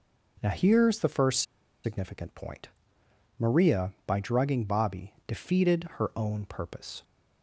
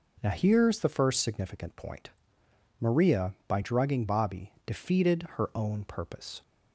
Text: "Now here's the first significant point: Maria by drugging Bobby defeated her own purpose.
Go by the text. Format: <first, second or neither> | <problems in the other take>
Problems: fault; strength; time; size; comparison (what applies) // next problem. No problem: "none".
second | pauses between "first" and "significant"; at 1.4 s; 0.41 s long